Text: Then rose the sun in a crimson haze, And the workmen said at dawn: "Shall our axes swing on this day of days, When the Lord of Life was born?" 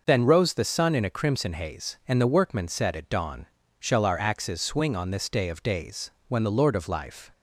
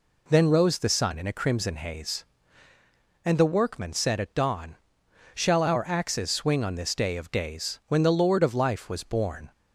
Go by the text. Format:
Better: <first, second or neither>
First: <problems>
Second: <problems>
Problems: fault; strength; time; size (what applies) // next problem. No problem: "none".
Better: second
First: stops before "was born"; at 7.3 s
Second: none